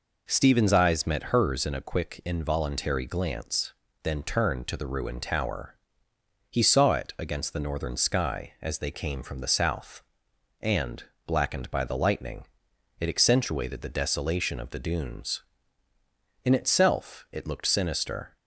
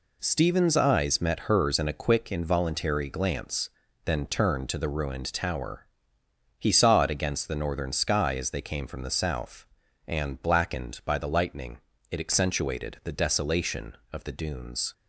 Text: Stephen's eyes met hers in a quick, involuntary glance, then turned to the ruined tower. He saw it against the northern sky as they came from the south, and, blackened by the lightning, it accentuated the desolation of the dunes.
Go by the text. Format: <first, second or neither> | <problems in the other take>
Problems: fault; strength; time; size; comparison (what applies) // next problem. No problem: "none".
second | goes on to say "In itself it looked sinister"; strong; from 16.4 s on; 1.9 s long